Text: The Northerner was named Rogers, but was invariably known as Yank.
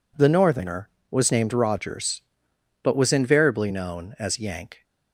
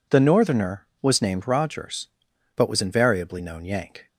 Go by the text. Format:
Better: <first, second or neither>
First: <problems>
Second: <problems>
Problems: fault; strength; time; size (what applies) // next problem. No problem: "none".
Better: first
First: none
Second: skips "as"; at 3.6 s